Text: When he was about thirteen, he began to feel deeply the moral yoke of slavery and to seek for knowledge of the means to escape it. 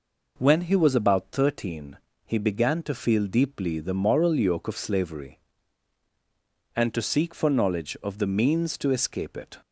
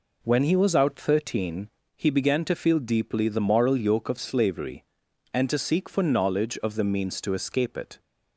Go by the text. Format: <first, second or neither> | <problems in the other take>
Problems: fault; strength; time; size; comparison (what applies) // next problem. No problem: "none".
first | says "out" for "about"; at 0.7 s